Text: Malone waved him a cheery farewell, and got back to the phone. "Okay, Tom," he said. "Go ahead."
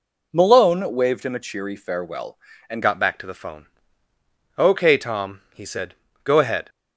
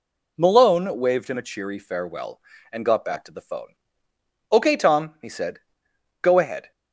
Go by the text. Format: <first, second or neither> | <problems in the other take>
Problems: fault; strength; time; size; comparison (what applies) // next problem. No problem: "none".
second | changes voice at "got"; from 2.8 s on; 3.8 s long